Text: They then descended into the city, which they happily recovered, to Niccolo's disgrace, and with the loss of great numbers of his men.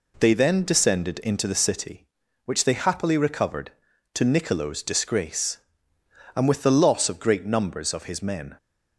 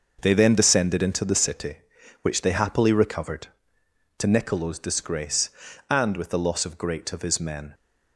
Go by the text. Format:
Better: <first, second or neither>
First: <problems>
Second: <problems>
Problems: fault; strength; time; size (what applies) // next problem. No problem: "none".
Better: first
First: none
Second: starts louder than the rest; noticeable; until 1.2 s; 6 dB // skips "numbers"; at 7.1 s